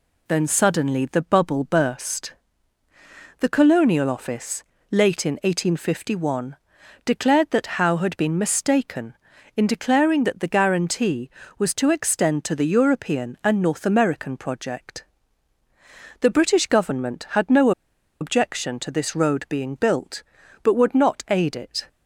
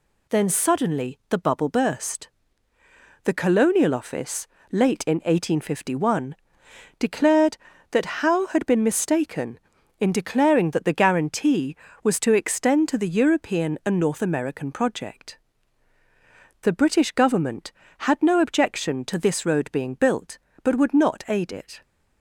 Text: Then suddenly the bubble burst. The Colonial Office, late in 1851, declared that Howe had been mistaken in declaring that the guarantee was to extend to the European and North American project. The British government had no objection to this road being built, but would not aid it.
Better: second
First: pauses between "no" and "objection"; noticeable; at 17.7 s; 0.50 s long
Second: none

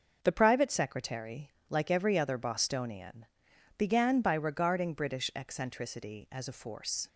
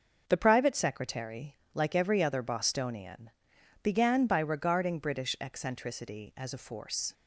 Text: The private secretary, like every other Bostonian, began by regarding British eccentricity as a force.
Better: neither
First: starts louder than the rest; noticeable; until 1.2 s; 6 dB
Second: starts louder than the rest; until 1.3 s; 6 dB

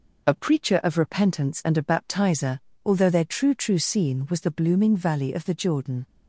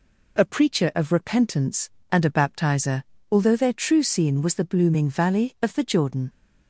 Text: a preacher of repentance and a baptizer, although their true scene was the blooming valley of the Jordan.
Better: second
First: says "true" twice; at 3.5 s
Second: none

